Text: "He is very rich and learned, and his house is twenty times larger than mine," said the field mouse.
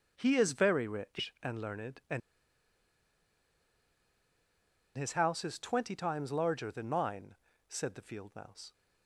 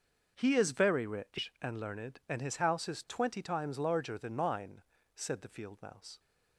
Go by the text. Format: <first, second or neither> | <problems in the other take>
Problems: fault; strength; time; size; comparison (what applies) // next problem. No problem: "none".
second | starts louder than the rest; until 1.1 s; 6.5 dB; also in the second // pauses between "and" and "his"; strong; at 2.2 s; 2.7 s long